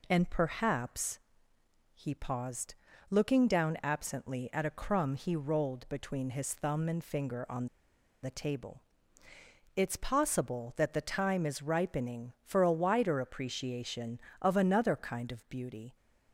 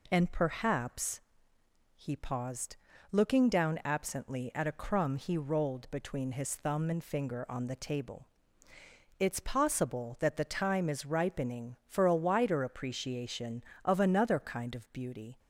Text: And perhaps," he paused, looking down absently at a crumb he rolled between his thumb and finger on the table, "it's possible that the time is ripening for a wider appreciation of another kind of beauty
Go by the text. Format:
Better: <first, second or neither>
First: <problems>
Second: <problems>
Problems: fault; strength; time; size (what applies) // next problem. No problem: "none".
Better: second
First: pauses between "on" and "the"; noticeable; at 7.6 s; 0.55 s long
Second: none